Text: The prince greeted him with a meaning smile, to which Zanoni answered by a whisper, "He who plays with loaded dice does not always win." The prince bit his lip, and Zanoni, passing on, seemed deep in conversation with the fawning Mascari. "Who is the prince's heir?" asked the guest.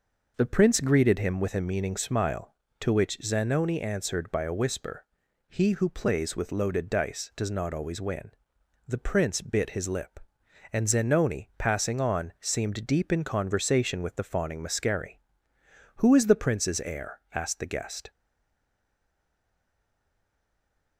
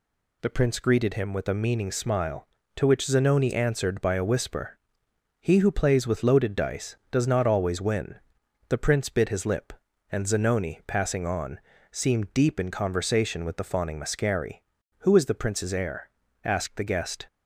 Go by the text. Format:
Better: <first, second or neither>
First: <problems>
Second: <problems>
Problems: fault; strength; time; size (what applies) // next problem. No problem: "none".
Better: second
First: stays silent after the last word; strong; from 18.1 s on; 2.8 s long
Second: none